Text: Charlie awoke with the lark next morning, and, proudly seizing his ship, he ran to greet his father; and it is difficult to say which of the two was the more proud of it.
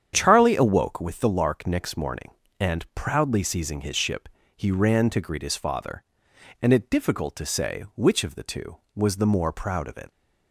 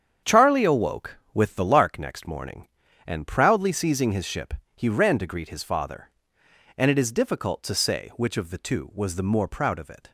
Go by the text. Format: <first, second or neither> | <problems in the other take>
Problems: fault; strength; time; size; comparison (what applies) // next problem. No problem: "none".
second | starts louder than the rest; strong; until 1.1 s; 8.5 dB; strong in the second // skips "is"; at 6.8 s